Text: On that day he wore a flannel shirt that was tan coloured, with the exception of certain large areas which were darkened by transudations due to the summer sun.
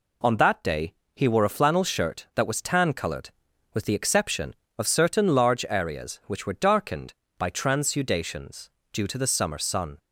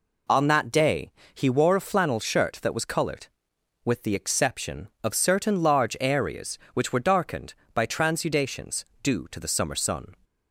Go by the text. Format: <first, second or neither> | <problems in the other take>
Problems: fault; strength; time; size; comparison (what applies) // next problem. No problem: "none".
first | pauses between "day" and "he"; slight; at 1.1 s; 0.22 s long; slight in the first // skips "tan"; at 2.8 s // pauses between "transudations" and "due"; slight; at 8.8 s; 0.18 s long; slight in the first